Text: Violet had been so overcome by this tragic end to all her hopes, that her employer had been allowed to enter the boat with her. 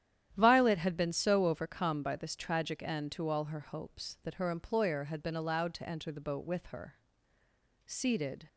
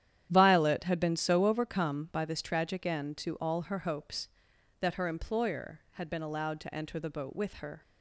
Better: second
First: starts louder than the rest; strong; until 1.3 s; 11 dB // goes on to say "Seated"; noticeable; from 7.8 s on; 0.62 s long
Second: starts louder than the rest; strong; until 1.3 s; 10.5 dB

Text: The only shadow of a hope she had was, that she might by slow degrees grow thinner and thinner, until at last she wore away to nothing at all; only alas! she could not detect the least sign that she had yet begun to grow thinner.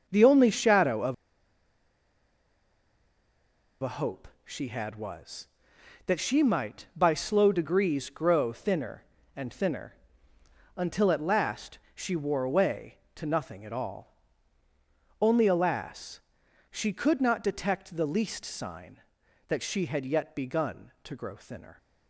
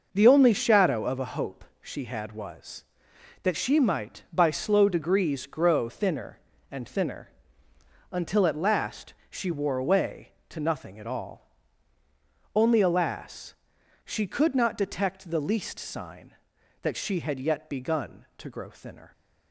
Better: second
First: starts louder than the rest; noticeable; until 1.0 s; 6 dB // pauses between "of" and "a"; strong; at 1.1 s; 2.6 s long // pauses between "hope" and "she"; slight; at 4.2 s; 0.16 s long // pauses between "last" and "she"; slight; at 11.7 s; 0.16 s long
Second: starts louder than the rest; noticeable; until 1.1 s; 6 dB // pauses between "hope" and "she"; slight; at 1.6 s; 0.16 s long // pauses between "last" and "she"; slight; at 9.1 s; 0.16 s long

